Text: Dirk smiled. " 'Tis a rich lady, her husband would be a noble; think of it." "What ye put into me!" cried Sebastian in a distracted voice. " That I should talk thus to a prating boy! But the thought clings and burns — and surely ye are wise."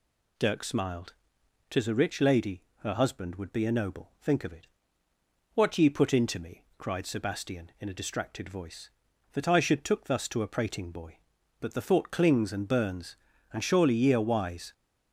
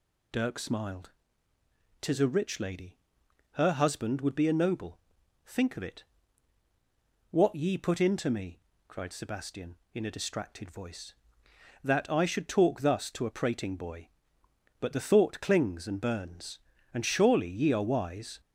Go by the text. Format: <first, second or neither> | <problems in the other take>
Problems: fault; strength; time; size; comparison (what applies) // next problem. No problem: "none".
second | says "took" for "talk"; at 9.8 s